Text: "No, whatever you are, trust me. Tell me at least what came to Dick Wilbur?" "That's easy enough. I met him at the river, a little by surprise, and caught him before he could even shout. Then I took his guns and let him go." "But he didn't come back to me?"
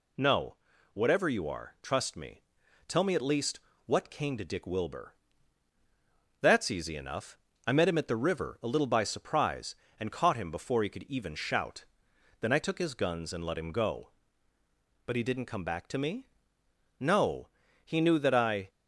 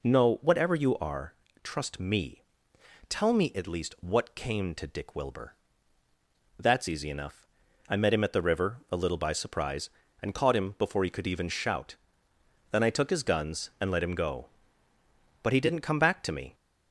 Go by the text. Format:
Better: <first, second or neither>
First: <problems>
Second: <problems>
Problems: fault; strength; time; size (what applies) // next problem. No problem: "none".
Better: second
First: pauses between "least" and "what"; slight; at 3.5 s; 0.26 s long // goes on to say "No He knew that I"; strong; from 16.9 s on; 1.7 s long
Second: none